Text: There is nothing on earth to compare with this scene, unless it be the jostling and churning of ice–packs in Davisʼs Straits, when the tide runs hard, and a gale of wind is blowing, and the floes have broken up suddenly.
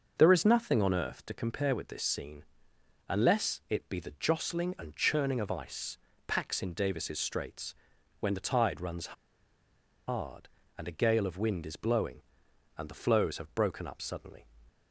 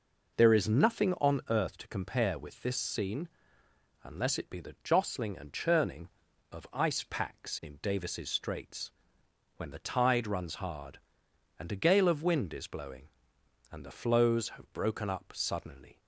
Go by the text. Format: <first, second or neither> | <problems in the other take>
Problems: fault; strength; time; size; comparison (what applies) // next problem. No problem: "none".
second | starts louder than the rest; until 1.1 s; 6.5 dB // pauses between "runs" and "hard"; noticeable; at 9.1 s; 0.93 s long